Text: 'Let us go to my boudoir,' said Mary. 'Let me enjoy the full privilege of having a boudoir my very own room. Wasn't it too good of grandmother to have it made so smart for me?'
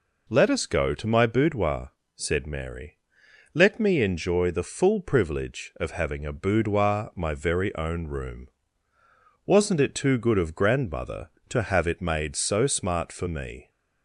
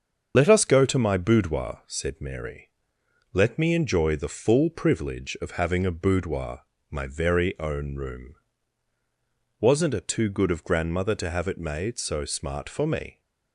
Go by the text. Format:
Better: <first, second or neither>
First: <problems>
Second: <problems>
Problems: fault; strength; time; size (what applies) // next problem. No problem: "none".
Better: first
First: none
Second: loses the start of "Let"; at 0.3 s; 55 ms // starts louder than the rest; strong; until 1.3 s; 7 dB // pauses between "boudoir" and "my"; slight; at 6.6 s; 0.28 s long